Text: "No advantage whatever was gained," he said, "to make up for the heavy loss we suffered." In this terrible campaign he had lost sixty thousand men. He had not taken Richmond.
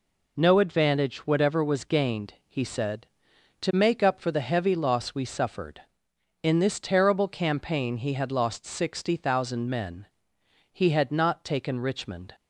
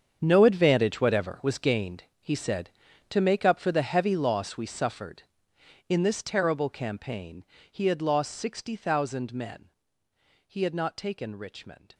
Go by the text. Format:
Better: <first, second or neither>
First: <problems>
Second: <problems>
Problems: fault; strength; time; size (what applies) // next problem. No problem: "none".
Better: first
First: none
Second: gets quieter; strong; throughout; 14.5 dB // pauses between "campaign" and "he"; slight; at 7.4 s; 0.26 s long